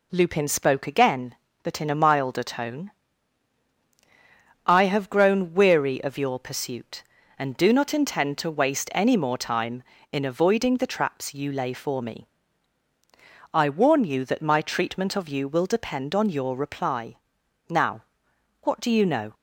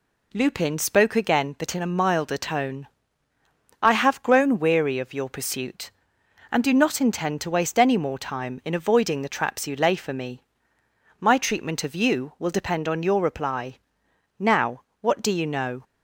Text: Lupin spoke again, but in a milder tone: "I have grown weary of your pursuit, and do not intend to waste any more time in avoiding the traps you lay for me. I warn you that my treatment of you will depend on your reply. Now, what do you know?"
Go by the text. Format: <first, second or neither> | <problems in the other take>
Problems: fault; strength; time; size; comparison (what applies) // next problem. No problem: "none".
first | skips "I warn you that"; at 10.7 s